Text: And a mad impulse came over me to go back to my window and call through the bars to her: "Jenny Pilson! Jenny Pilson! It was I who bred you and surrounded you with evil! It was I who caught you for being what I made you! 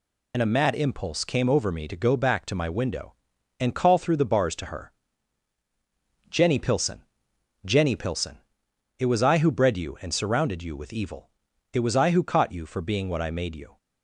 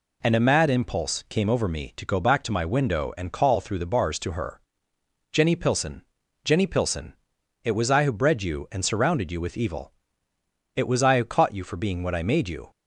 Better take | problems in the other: second | loses the start of "And"; at 0.3 s; 55 ms

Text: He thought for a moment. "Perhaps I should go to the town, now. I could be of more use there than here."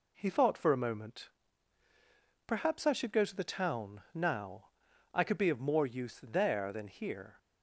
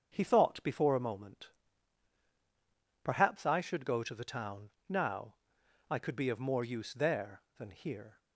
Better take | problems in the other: first | starts louder than the rest; until 1.1 s; 7 dB // says "before" for "for"; at 0.6 s

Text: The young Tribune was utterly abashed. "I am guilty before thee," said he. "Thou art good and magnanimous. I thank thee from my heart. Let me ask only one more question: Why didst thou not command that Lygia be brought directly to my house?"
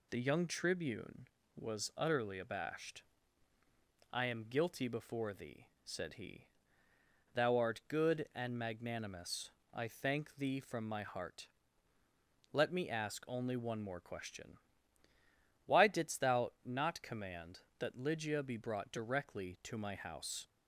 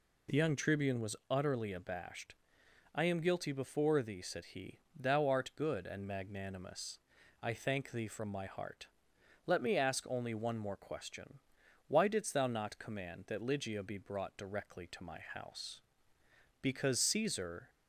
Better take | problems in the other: first | goes on to say "Because Caesar"; noticeable; from 16.5 s on; 1.1 s long

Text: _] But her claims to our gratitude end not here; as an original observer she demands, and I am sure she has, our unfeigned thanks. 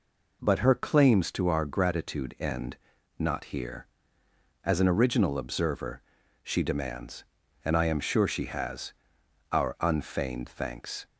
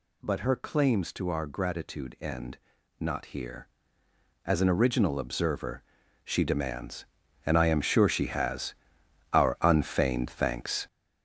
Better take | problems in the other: first | gets louder; strong; throughout; 7.5 dB // pauses between "end" and "not"; at 2.5 s; 0.40 s long; also in the first // pauses between "observer" and "she"; at 5.8 s; 0.42 s long; also in the first

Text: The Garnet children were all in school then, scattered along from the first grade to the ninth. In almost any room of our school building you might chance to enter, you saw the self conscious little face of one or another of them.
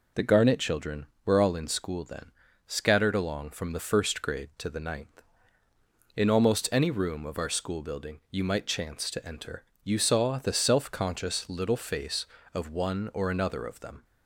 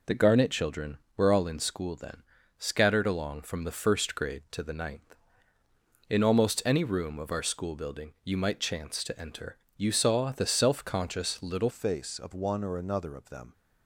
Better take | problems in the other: first | changes voice at "face"; from 11.6 s on; 1.9 s long

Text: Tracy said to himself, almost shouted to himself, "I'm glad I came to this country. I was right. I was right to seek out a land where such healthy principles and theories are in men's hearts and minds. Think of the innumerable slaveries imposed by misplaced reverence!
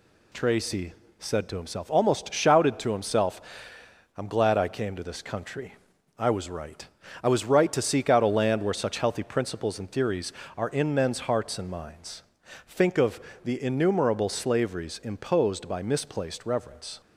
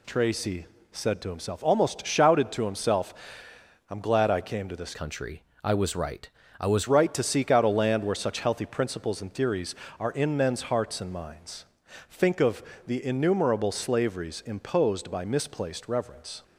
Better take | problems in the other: first | pauses between "Tracy" and "said"; slight; at 0.6 s; 0.26 s long; slight in the first // changes voice from "country" to "was"; from 4.9 to 6.8 s; 1.9 s long // pauses between "of" and "the"; slight; at 12.6 s; 0.24 s long; slight in the first

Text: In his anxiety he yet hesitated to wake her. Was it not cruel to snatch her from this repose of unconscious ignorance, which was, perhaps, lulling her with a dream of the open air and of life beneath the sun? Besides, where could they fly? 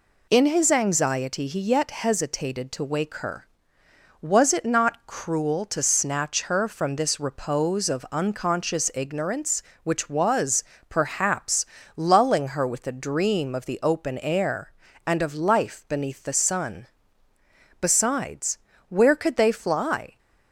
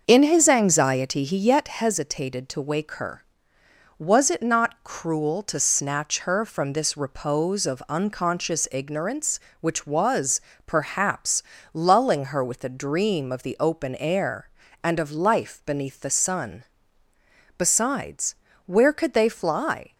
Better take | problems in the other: first | starts louder than the rest; until 1.8 s; 6.5 dB

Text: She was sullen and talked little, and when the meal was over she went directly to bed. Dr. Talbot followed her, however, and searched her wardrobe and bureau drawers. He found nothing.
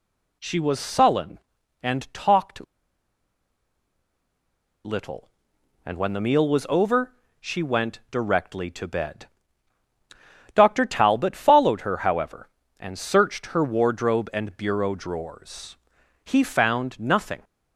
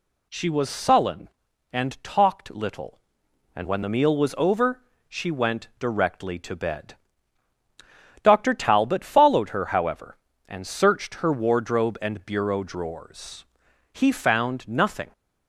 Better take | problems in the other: second | pauses between "talked" and "little"; strong; at 2.6 s; 2.2 s long // pauses between "over" and "she"; slight; at 7.1 s; 0.26 s long; slight in the second

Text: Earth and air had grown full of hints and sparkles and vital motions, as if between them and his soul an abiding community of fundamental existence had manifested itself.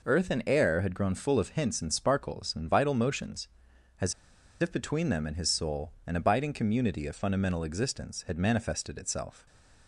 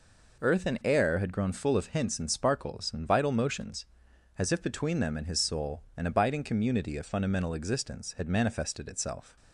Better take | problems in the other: second | pauses between "as" and "if"; noticeable; at 4.1 s; 0.48 s long // pauses between "soul" and "an"; slight; at 5.9 s; 0.16 s long; slight in the second // stays silent after the last word; slight; from 9.3 s on; 0.5 s long

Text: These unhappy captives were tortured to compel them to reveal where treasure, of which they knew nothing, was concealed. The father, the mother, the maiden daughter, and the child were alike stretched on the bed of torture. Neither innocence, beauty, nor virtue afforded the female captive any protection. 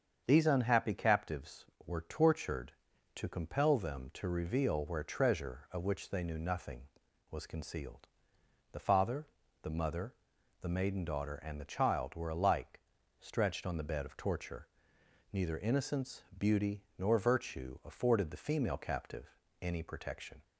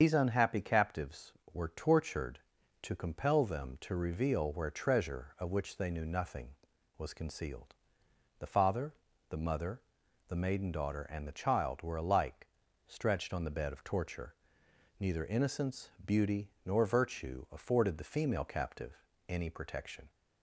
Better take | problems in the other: first | loses the start of "These"; at 0.0 s; 70 ms // starts louder than the rest; until 1.0 s; 7 dB; strong in the first // pauses between "alike" and "stretched"; at 12.4 s; 0.38 s long; also in the first // pauses between "captive" and "any"; slight; at 18.9 s; 0.30 s long; slight in the first

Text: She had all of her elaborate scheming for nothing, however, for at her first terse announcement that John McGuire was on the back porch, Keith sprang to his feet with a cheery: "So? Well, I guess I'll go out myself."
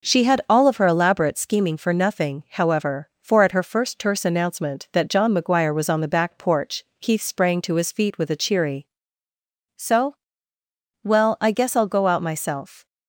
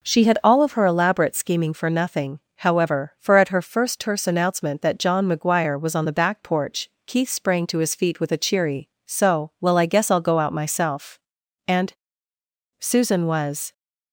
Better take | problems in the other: first | goes on to say "And Susan was"; strong; from 11.6 s on; 2.0 s long

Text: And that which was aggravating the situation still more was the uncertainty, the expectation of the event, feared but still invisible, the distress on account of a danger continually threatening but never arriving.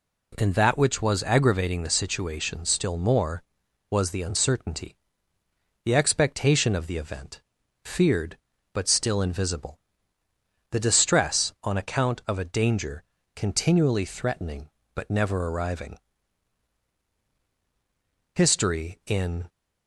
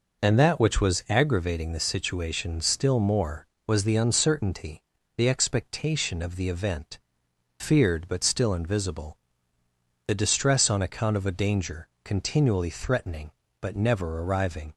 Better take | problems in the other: second | pauses between "danger" and "continually"; slight; at 13.0 s; 0.32 s long; slight in the second // goes on to say "History in"; noticeable; from 18.3 s on; 1.1 s long

